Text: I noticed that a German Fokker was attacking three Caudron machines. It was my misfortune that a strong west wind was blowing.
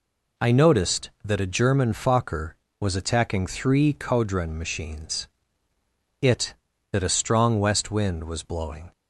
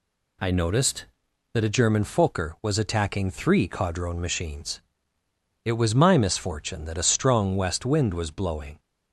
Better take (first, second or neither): second